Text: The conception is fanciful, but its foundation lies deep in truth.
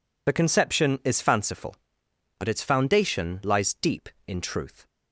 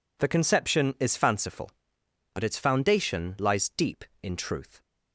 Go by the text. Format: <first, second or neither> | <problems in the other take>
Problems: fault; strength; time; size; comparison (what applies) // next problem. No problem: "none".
second | loses the start of "The"; at 0.2 s; 30 ms